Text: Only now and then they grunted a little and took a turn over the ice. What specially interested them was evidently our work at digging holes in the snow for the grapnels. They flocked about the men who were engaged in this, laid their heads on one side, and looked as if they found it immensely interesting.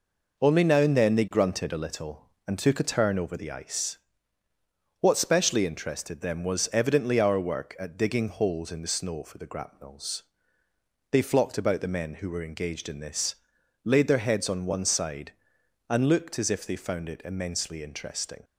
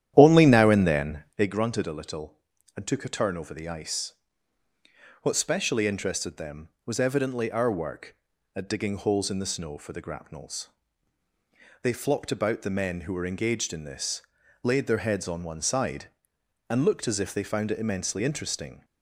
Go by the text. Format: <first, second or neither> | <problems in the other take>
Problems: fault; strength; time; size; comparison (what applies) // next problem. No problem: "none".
first | starts louder than the rest; strong; until 1.6 s; 11 dB